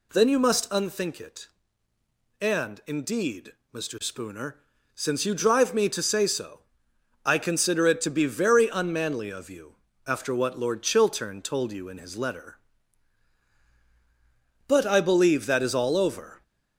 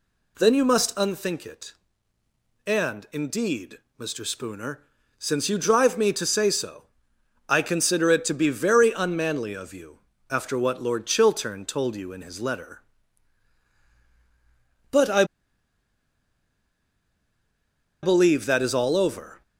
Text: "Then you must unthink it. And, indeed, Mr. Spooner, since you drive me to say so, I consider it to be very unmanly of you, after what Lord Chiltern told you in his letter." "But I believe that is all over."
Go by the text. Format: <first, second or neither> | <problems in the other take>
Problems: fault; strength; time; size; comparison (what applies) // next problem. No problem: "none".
first | pauses between "I" and "believe"; strong; at 15.2 s; 2.7 s long